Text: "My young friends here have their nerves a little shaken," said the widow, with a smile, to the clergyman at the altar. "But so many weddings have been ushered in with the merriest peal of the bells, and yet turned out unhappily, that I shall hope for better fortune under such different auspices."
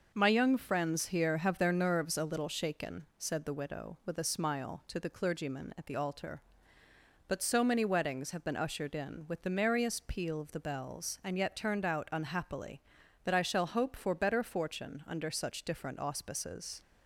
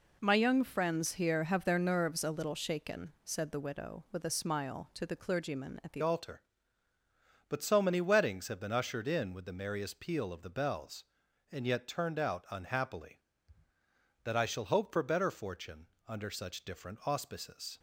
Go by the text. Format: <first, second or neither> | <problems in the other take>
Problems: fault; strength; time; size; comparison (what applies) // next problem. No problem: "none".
first | changes voice at "altar"; from 6.0 s on; 11.7 s long // pauses between "fortune" and "under"; slight; at 15.8 s; 0.20 s long